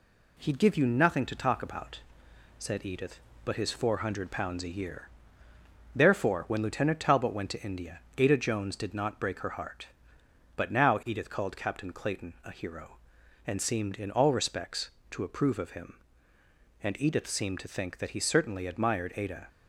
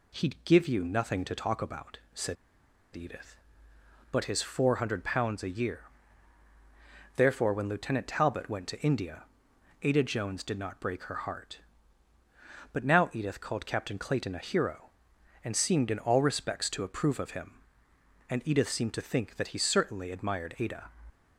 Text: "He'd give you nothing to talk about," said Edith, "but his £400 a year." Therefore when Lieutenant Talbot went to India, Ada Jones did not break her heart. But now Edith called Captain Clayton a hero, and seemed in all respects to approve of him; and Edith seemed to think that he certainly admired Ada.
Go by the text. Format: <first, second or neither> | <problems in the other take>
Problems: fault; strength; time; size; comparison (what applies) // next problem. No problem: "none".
first | pauses between "said" and "Edith"; noticeable; at 2.3 s; 0.59 s long